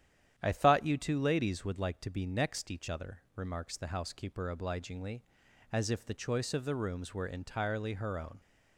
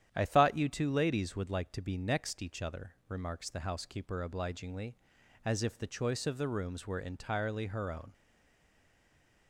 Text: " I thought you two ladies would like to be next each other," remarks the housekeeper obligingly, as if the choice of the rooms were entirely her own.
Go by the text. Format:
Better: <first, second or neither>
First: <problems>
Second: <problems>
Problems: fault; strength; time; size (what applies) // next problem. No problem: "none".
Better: first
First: starts louder than the rest; strong; until 1.3 s; 10 dB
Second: starts louder than the rest; strong; until 1.1 s; 10 dB // stays silent after the last word; noticeable; from 8.1 s on; 1.3 s long